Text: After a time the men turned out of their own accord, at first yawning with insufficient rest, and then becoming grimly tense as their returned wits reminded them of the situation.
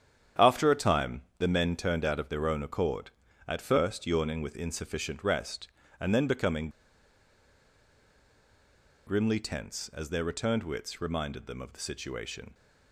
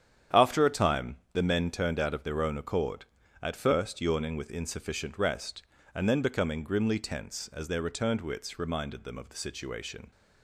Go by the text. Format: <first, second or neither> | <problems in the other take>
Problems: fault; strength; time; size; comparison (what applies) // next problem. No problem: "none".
second | starts louder than the rest; strong; until 1.5 s; 9 dB; strong in the second // pauses between "time" and "the"; slight; at 1.2 s; 0.16 s long; slight in the second // pauses between "becoming" and "grimly"; strong; at 6.6 s; 2.3 s long